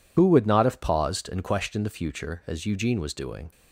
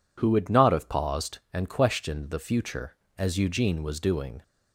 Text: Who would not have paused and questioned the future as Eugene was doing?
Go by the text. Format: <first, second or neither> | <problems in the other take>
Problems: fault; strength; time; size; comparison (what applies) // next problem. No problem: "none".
second | loses the start of "Who"; at 0.1 s; 60 ms